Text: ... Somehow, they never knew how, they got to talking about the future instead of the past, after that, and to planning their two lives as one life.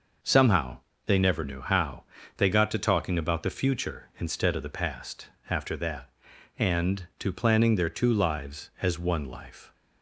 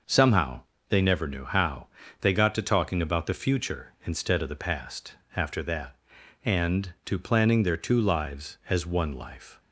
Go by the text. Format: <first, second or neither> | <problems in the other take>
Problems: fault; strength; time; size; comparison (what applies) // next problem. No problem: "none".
neither | none